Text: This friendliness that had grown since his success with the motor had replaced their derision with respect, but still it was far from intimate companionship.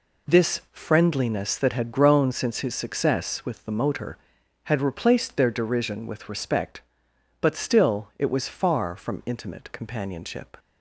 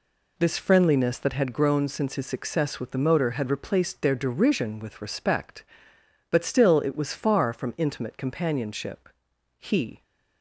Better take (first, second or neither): first